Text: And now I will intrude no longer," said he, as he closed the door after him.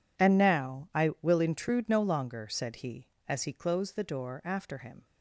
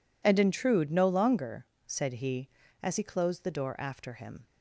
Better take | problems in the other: first | skips "now I will"; at 0.3 s

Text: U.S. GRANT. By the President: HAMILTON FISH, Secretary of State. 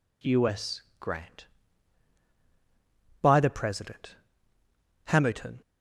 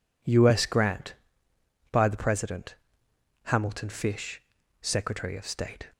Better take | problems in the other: second | stops before "FISH Secretary of State"; at 5.6 s

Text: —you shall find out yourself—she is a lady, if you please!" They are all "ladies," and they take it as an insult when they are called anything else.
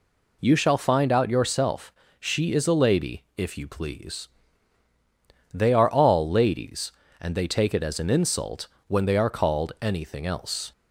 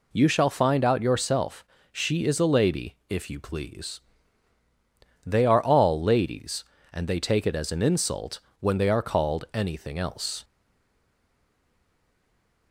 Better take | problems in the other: first | pauses between "insult" and "when"; slight; at 8.3 s; 0.20 s long; slight in the first // stays silent after the last word; from 10.4 s on; 2.3 s long

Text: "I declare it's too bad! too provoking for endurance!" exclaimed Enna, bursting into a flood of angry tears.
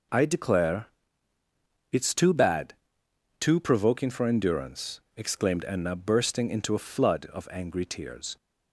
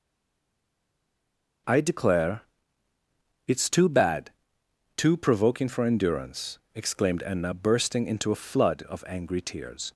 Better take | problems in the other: first | stays silent before the first word; noticeable; until 1.6 s; 1.6 s long // pauses between "declare" and "it's"; at 2.4 s; 1.0 s long; also in the first

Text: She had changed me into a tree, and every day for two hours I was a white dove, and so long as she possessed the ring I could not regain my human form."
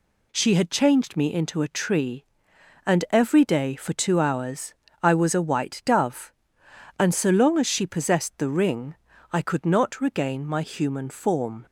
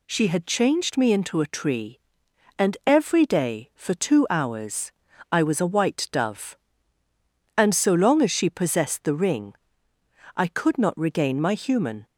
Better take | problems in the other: first | pauses between "hours" and "I"; at 4.9 s; 0.40 s long; slight in the first // pauses between "ring" and "I"; noticeable; at 9.5 s; 0.84 s long; slight in the first // stops before "form"; at 12.0 s

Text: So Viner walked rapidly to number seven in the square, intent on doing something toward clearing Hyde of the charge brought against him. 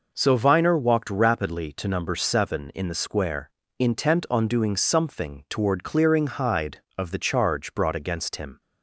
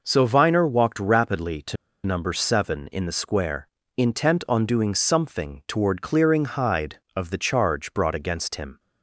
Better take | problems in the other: first | pauses between "to" and "number"; slight; at 1.7 s; 0.29 s long

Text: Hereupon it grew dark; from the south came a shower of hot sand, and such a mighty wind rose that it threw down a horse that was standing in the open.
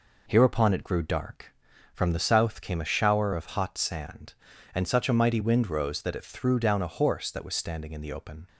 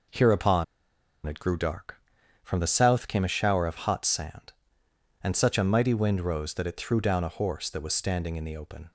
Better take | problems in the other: first | pauses between "Hereupon" and "it"; noticeable; at 0.6 s; 0.61 s long

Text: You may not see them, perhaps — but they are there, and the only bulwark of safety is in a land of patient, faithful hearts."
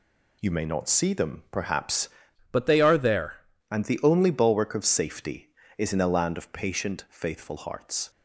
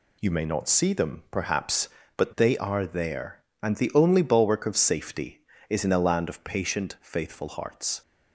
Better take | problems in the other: second | changes voice from "but" to "there"; from 2.5 to 3.4 s; 0.9 s long

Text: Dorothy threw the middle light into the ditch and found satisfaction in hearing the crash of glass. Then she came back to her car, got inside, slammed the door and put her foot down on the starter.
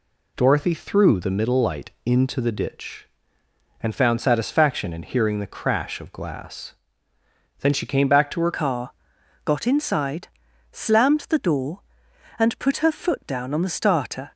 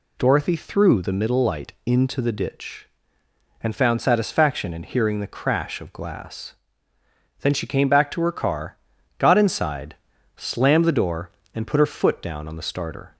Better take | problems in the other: second | changes voice at "car"; from 8.5 s on; 5.8 s long

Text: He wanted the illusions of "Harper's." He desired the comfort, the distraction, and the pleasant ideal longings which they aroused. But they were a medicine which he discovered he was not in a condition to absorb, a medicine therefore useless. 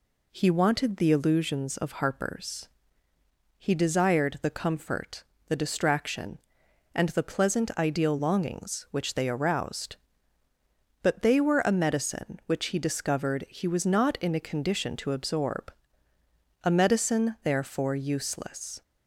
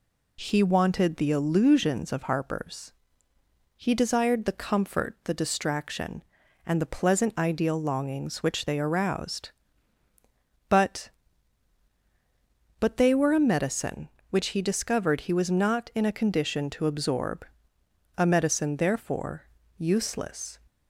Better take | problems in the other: first | says "But" twice; at 12.7 s // pauses between "therefore" and "useless"; slight; at 19.4 s; 0.28 s long

